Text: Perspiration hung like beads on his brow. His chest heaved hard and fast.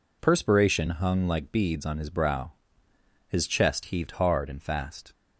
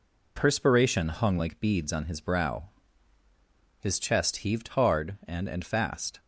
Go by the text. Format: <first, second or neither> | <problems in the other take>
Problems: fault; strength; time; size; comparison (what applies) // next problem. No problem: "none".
first | says "and" twice; at 5.4 s